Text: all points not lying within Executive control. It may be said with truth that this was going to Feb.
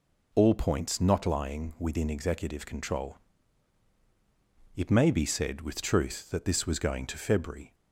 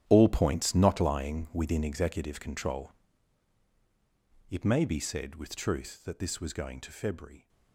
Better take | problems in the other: first | gets quieter; strong; throughout; 14 dB

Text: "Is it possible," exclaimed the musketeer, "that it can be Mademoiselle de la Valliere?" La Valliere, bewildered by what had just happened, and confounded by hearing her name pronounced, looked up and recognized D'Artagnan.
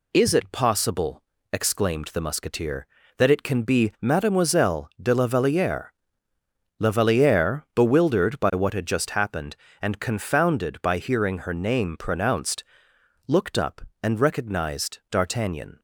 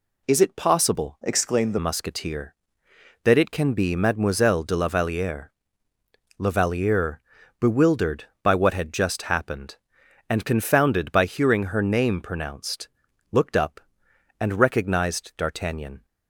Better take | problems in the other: first | changes voice from "exclaimed" to "the"; from 1.2 to 1.7 s; 0.5 s long

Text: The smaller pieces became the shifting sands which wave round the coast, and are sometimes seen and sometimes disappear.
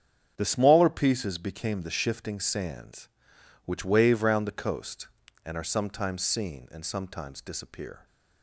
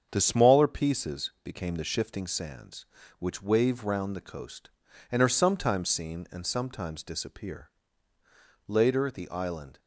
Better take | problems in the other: first | starts louder than the rest; strong; until 1.1 s; 7.5 dB; strong in the first // goes on to say "Later the island"; noticeable; from 8.6 s on; 1.1 s long

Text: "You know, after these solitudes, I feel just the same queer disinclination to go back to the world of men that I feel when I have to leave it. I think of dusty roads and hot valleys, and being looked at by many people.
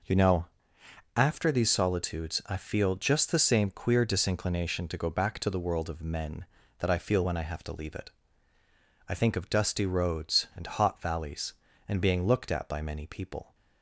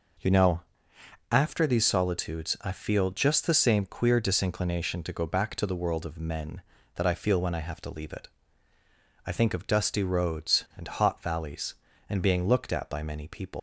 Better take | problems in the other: first | leaves "people" unfinished; at 13.5 s; 155 ms

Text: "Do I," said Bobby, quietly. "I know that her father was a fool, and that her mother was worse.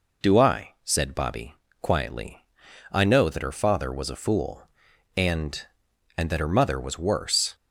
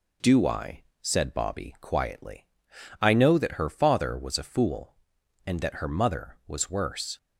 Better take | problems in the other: second | says "and" twice; at 6.1 s

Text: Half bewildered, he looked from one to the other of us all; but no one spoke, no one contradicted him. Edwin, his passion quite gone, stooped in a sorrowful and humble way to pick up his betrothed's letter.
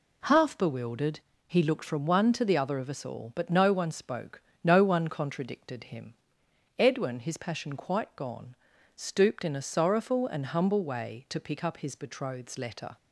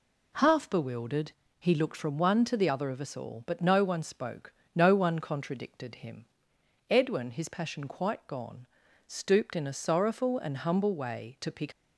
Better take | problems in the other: first | stops before "up his betrothed's letter"; at 11.7 s

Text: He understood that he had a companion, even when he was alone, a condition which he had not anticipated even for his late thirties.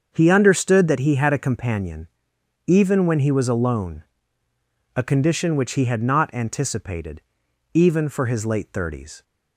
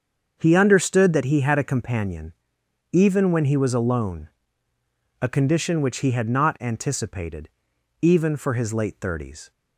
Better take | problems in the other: neither | starts louder than the rest; the same in both // pauses between "anticipated" and "even"; noticeable; the same in both

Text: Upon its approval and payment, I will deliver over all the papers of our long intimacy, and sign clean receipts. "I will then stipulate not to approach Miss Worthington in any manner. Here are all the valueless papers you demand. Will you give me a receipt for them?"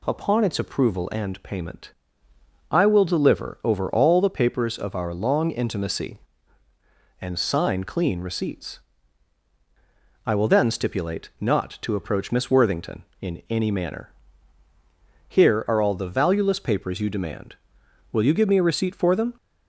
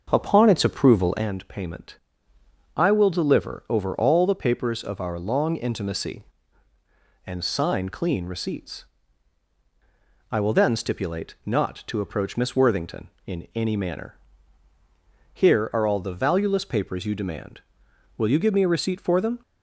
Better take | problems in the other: first | starts louder than the rest; until 1.3 s; 6 dB

